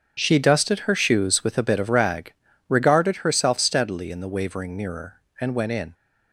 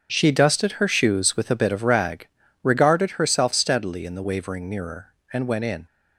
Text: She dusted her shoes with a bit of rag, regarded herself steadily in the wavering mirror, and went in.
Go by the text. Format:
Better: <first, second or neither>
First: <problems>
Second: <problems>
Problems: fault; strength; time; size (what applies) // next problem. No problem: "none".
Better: neither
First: starts louder than the rest; until 1.1 s; 7 dB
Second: starts louder than the rest; until 1.1 s; 7 dB